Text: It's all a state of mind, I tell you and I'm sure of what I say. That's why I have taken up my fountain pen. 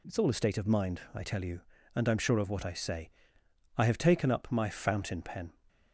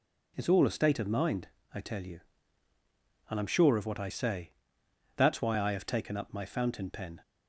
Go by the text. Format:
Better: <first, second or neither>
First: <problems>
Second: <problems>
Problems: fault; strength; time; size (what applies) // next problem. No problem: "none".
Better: second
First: skips "That's why"; at 3.4 s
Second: none